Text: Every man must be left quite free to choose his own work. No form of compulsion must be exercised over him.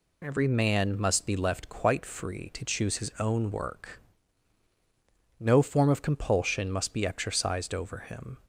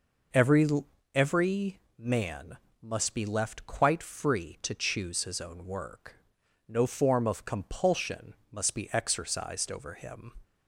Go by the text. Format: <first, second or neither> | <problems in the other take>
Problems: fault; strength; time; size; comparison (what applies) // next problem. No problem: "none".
first | says "Every" twice; at 1.1 s // pauses between "man" and "must"; slight; at 2.5 s; 0.24 s long // pauses between "compulsion" and "must"; slight; at 8.3 s; 0.16 s long